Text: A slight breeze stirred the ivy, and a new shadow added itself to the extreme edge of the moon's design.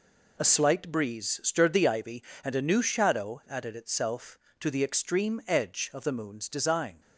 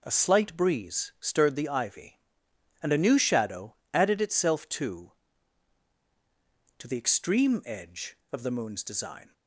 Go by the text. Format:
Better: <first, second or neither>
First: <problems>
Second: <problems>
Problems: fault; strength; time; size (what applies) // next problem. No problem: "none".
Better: first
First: none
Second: pauses between "shadow" and "added"; slight; at 3.7 s; 0.18 s long // says "to" twice; at 6.7 s